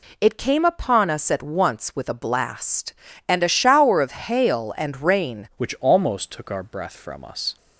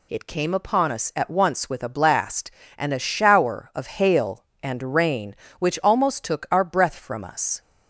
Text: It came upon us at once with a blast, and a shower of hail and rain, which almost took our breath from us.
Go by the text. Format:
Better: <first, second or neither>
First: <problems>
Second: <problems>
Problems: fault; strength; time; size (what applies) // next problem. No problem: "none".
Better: second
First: changes voice at "which"; from 5.5 s on; 2.0 s long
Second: none